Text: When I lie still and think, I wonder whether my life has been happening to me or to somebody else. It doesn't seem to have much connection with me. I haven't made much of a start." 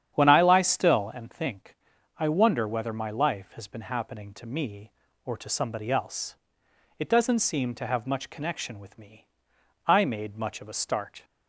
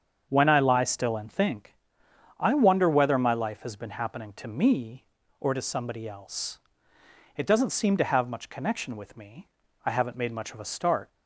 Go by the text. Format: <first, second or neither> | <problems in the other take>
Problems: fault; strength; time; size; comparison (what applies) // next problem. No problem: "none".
second | starts louder than the rest; strong; until 1.1 s; 9 dB; strong in the second // skips "haven't"; at 10.0 s